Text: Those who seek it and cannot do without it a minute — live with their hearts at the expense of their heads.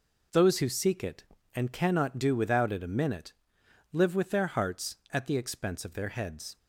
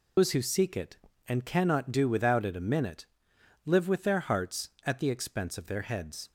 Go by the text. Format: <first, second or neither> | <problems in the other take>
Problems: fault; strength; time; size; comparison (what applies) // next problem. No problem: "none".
first | loses the start of "Those"; at 0.1 s; 125 ms